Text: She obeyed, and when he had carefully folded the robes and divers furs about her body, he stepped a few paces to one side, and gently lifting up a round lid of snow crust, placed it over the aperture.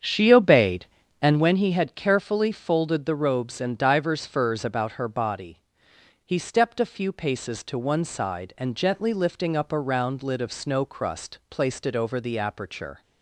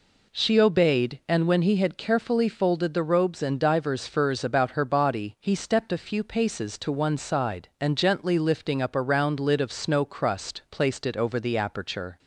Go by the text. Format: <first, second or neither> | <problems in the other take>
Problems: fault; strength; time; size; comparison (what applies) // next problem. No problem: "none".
second | starts louder than the rest; strong; until 1.6 s; 8 dB